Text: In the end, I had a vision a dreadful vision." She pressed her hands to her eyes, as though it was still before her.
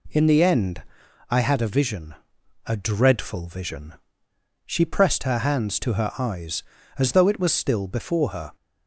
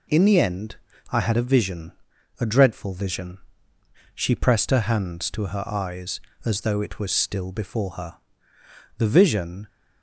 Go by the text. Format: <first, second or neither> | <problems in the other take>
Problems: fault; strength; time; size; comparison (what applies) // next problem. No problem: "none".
first | pauses between "vision" and "a"; noticeable; at 1.9 s; 0.48 s long; noticeable in the first // goes on to say "The vision"; noticeable; from 8.9 s on; 0.68 s long